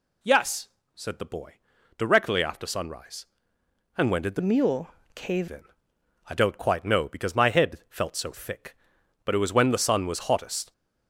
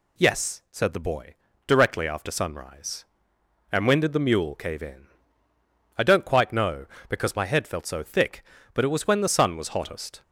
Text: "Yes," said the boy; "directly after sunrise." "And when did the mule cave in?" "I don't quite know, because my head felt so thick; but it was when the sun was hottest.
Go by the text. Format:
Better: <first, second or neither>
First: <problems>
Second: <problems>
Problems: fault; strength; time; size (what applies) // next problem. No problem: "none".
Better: second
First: changes voice from "mule" to "cave"; from 4.3 to 5.4 s; 1.1 s long // pauses between "mule" and "cave"; slight; at 4.8 s; 0.24 s long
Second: none